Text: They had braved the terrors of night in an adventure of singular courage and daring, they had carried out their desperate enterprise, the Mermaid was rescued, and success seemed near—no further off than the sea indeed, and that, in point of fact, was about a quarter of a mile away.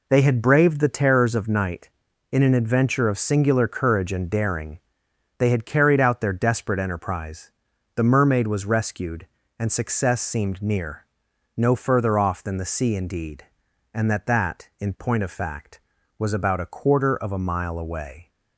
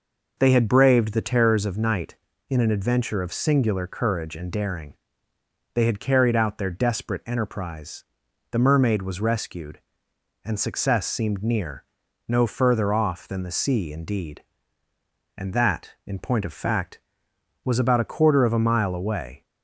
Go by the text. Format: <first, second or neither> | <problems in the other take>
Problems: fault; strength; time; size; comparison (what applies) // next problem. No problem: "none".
second | says "that" twice; at 14.2 s